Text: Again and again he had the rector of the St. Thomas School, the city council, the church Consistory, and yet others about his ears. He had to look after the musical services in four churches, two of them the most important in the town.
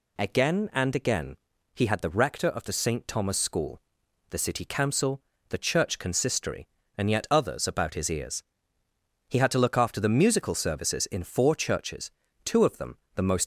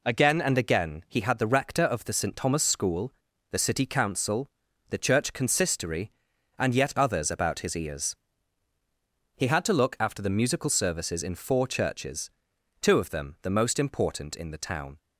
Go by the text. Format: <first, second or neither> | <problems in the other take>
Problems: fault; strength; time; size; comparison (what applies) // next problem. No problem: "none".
second | pauses between "again" and "he"; at 1.3 s; 0.40 s long // pauses between "them" and "the"; slight; at 12.9 s; 0.18 s long // stops before "important in the town"; at 13.4 s